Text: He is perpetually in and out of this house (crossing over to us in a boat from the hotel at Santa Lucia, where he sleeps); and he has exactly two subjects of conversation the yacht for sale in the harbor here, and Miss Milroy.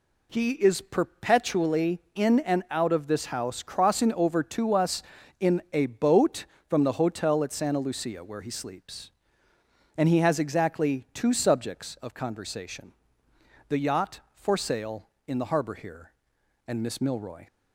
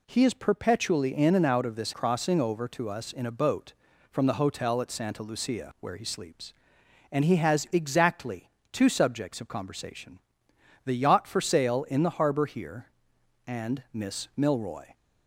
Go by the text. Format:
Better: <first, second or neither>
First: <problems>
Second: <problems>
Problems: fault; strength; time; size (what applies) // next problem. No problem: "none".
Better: first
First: pauses between "conversation" and "the"; noticeable; at 12.9 s; 0.74 s long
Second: skips "house"; at 1.9 s // pauses between "exactly" and "two"; slight; at 8.5 s; 0.22 s long // pauses between "conversation" and "the"; noticeable; at 10.1 s; 0.66 s long